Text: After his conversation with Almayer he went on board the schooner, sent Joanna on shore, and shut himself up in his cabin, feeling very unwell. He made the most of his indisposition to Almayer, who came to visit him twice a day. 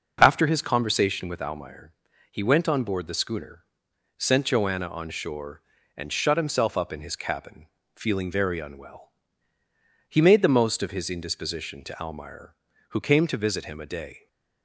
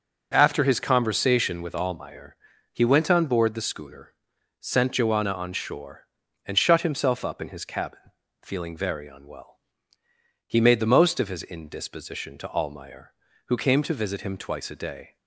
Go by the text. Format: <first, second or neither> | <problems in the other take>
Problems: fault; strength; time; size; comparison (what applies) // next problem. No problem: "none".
second | pauses between "Almayer" and "he"; at 1.9 s; 0.38 s long; slight in the second // skips "twice"; at 13.7 s